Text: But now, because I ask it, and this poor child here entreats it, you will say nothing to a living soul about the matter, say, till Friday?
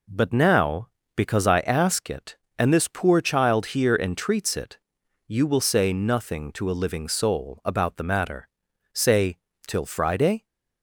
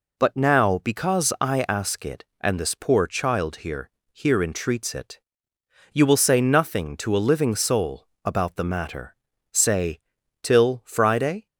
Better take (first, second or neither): first